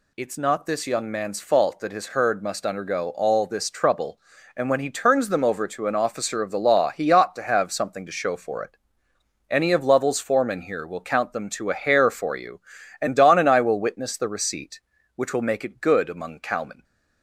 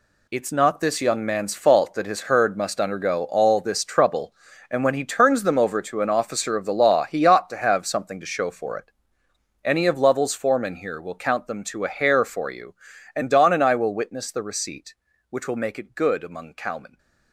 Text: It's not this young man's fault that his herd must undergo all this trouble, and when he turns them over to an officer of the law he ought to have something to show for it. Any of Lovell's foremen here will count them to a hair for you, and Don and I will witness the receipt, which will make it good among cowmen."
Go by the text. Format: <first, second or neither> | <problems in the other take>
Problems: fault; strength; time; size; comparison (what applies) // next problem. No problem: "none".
first | gets quieter; strong; throughout; 10 dB